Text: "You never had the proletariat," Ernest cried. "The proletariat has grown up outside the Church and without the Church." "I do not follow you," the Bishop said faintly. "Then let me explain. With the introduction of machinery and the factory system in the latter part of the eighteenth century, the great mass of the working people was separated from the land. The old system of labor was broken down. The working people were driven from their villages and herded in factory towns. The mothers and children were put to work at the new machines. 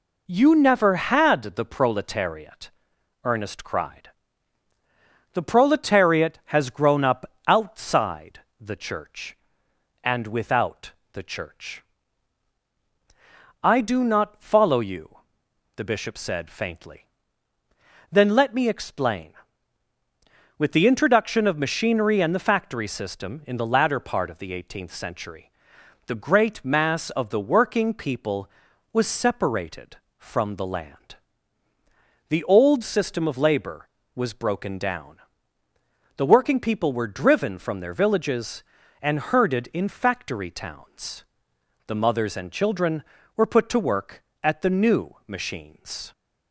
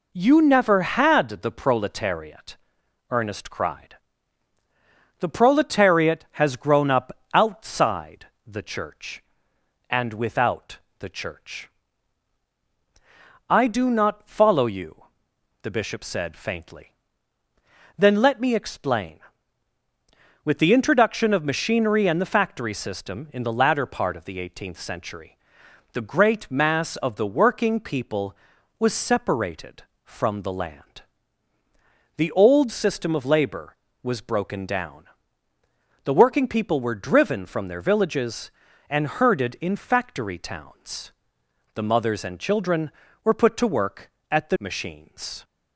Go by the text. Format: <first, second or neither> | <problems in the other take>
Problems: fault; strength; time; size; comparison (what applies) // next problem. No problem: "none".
first | pauses between "up" and "outside"; slight; at 7.1 s; 0.22 s long; slight in the first // pauses between "outside" and "the"; slight; at 8.2 s; 0.18 s long; slight in the first // pauses between "without" and "the"; slight; at 10.7 s; 0.22 s long; slight in the first // skips "new"; at 44.5 s